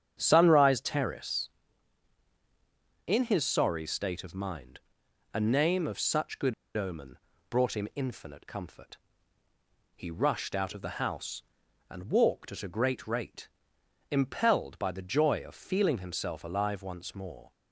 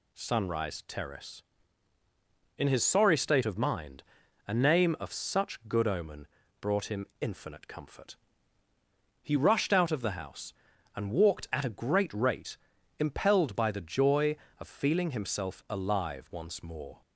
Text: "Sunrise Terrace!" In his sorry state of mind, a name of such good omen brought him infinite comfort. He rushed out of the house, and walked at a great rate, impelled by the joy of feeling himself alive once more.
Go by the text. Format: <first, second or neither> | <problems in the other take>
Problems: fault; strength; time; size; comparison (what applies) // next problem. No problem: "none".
second | starts louder than the rest; strong; until 1.2 s; 8 dB // pauses between "good" and "omen"; slight; at 6.5 s; 0.23 s long // pauses between "omen" and "brought"; slight; at 7.1 s; 0.32 s long; slight in the second